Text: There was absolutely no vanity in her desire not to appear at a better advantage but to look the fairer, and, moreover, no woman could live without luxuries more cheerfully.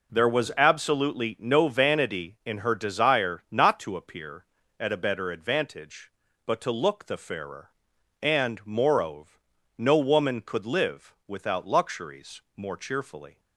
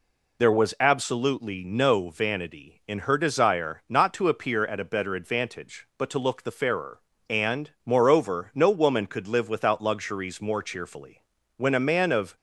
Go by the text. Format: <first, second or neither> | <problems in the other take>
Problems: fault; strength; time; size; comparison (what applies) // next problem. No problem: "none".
first | goes on to say "When a man of"; noticeable; from 11.5 s on; 0.78 s long